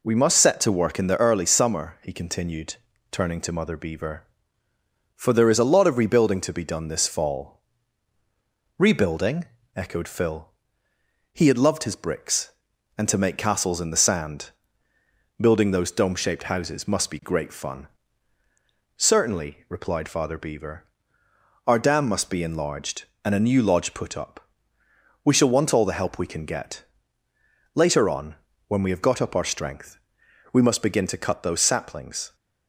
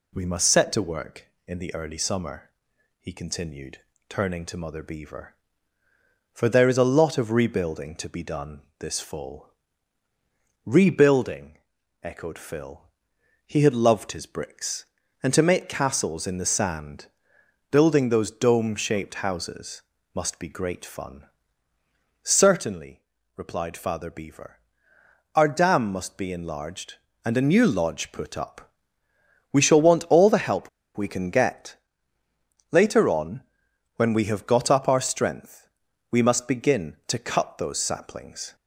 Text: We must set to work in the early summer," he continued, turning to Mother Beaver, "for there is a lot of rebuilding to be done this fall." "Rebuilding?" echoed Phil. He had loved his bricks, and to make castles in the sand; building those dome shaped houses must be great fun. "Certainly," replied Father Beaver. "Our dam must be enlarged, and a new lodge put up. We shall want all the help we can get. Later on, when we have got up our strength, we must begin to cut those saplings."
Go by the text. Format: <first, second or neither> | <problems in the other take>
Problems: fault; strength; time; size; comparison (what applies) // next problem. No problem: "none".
first | pauses between "done" and "this"; slight; at 8.6 s; 0.16 s long // pauses between "houses" and "must"; slight; at 19.8 s; 0.32 s long // pauses between "help" and "we"; slight; at 30.6 s; 0.27 s long